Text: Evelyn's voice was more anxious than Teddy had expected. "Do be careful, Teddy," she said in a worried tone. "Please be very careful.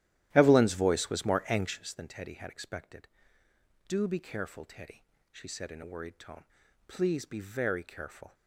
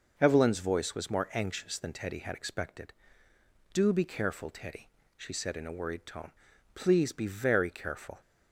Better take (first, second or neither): second